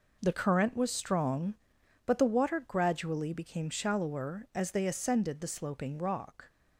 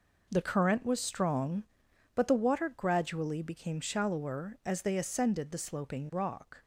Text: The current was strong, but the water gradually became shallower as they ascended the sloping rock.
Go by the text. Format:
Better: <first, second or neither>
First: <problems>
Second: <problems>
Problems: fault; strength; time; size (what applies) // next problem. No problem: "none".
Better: neither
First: none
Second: none